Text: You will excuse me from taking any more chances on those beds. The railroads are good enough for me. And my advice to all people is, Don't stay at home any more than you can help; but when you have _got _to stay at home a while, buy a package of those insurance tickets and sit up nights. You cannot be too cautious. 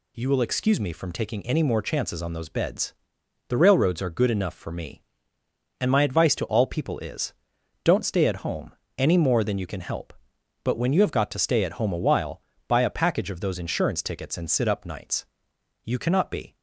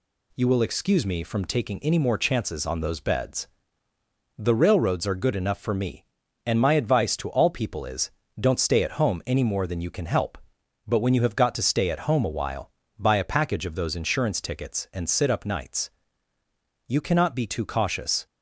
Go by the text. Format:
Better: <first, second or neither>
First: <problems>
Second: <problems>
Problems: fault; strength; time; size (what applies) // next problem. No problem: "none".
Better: second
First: pauses between "home" and "any"; slight; at 8.7 s; 0.24 s long // stops before "too cautious"; at 16.5 s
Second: none